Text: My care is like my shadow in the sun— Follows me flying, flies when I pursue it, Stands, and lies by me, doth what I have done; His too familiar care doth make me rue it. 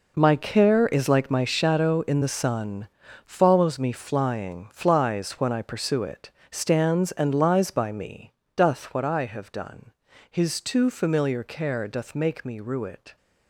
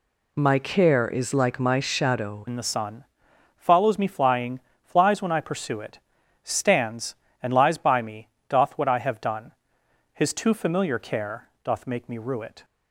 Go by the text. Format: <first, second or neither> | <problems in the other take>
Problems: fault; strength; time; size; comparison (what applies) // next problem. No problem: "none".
first | changes voice at "in"; from 2.4 s on; 10.2 s long // pauses between "care" and "doth"; slight; at 11.4 s; 0.16 s long